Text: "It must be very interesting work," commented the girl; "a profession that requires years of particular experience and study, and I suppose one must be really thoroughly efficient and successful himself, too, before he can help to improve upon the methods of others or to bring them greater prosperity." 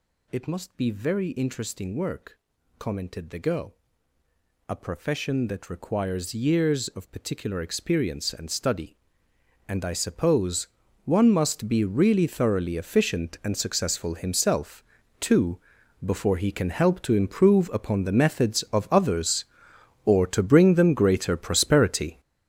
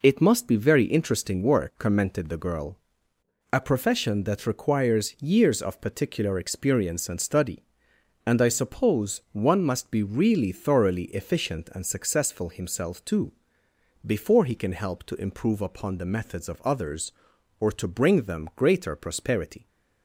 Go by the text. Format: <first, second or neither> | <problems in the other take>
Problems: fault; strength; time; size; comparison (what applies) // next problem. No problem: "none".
second | gets louder; strong; throughout; 11 dB // pauses between "suppose" and "one"; at 10.6 s; 0.38 s long